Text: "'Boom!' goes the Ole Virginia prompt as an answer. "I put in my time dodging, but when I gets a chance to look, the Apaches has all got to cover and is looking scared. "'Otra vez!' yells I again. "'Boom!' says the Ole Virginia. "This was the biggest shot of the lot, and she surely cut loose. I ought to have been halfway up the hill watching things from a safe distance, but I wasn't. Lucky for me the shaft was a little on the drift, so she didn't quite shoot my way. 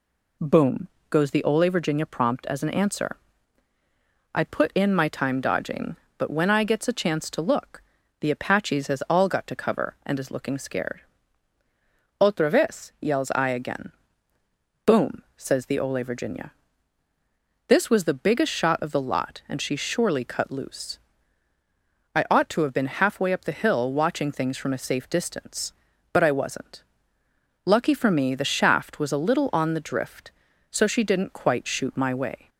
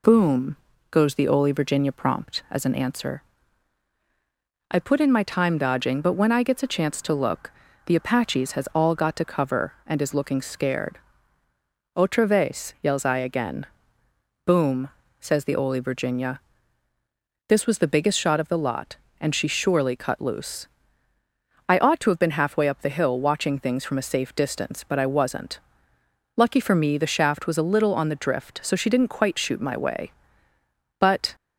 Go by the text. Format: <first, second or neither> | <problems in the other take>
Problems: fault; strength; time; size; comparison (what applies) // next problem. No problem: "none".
first | goes on to say "But"; slight; from 30.9 s on; 0.36 s long